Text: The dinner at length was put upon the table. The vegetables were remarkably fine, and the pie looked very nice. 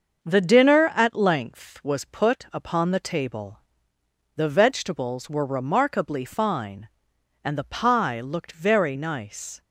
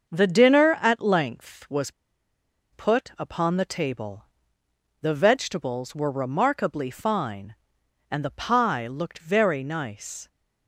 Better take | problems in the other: first | starts louder than the rest; until 1.1 s; 6.5 dB; also in the first // pauses between "was" and "put"; noticeable; at 1.9 s; 0.81 s long

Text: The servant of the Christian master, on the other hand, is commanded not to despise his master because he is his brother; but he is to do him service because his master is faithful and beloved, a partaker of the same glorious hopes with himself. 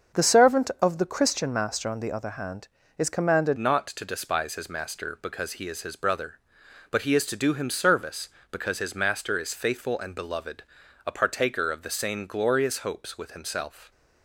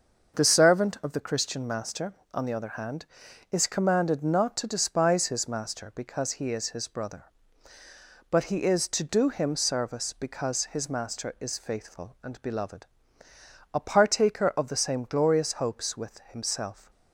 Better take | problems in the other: second | starts louder than the rest; until 1.2 s; 6.5 dB; also in the second // changes voice at "not"; from 3.5 s on; 10.4 s long

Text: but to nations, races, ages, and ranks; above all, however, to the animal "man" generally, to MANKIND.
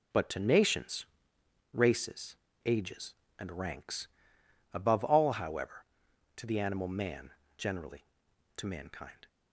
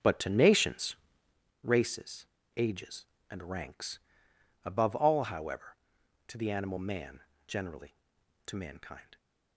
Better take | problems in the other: first | starts louder than the rest; strong; until 1.4 s; 7 dB // pauses between "man" and "generally"; slight; at 7.2 s; 0.26 s long; slight in the first

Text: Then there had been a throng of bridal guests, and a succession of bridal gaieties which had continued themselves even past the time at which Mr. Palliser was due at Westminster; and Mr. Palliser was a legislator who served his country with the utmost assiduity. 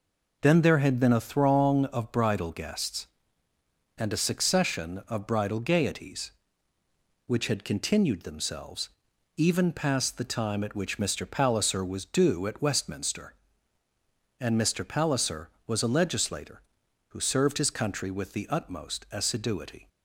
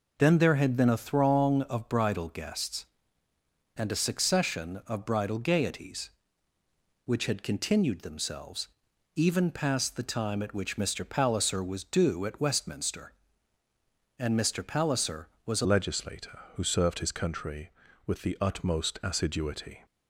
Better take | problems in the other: first | pauses between "themselves" and "even"; noticeable; at 8.6 s; 0.46 s long; noticeable in the first // changes voice at "legislator"; from 15.6 s on; 4.2 s long

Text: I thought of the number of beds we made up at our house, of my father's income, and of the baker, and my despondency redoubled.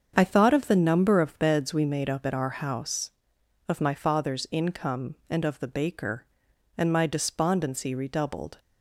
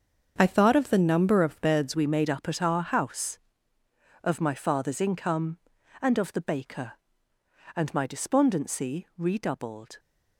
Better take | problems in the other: first | starts louder than the rest; until 1.3 s; 7 dB; also in the first // changes voice at "we"; from 1.9 s on; 8.0 s long

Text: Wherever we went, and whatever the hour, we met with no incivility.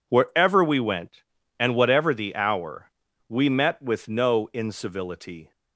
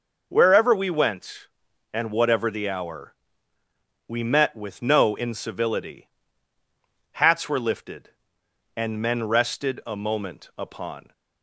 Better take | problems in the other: first | goes on to say "Hats were lifted and men rested a moment upon"; strong; from 7.1 s on; 4.0 s long

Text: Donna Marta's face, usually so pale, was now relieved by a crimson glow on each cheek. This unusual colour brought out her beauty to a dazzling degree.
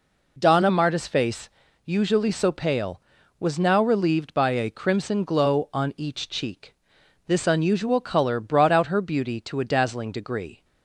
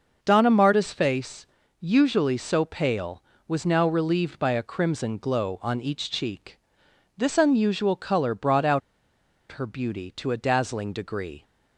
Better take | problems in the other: first | starts louder than the rest; noticeable; until 1.2 s; 6 dB // pauses between "out" and "her"; noticeable; at 8.8 s; 0.71 s long

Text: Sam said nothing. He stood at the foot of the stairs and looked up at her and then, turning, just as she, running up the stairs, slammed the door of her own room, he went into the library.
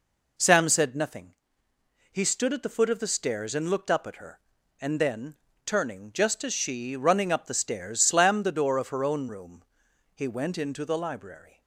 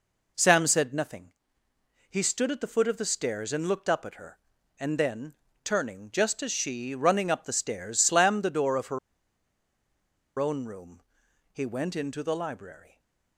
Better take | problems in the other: first | pauses between "her" and "own"; strong; at 8.9 s; 1.4 s long // stays silent after the last word; slight; from 12.8 s on; 0.5 s long

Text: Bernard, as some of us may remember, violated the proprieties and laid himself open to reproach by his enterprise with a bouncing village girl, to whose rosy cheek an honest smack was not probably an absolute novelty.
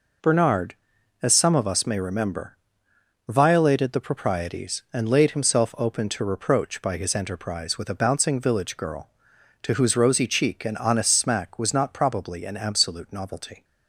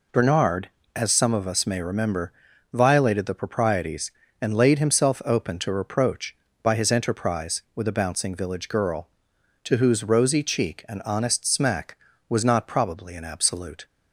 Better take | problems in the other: first | stops before "novelty"; at 13.8 s

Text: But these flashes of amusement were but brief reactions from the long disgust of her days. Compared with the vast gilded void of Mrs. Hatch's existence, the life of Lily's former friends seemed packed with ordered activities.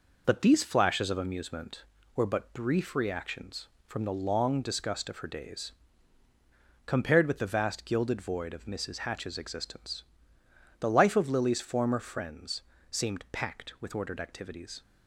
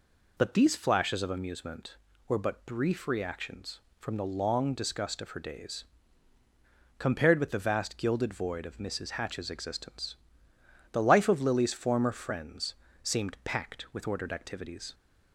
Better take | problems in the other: second | gets quieter; noticeable; throughout; 4.5 dB // pauses between "friends" and "seemed"; slight; at 12.6 s; 0.26 s long; slight in the second

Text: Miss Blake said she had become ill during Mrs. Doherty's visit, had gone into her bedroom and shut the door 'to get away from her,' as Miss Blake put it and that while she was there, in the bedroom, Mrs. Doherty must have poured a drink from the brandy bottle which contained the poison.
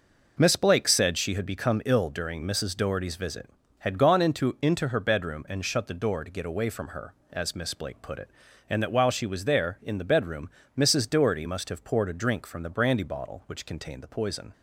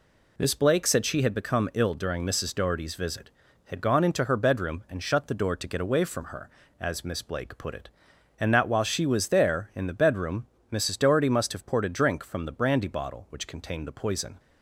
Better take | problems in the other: second | says "into" twice; at 4.6 s

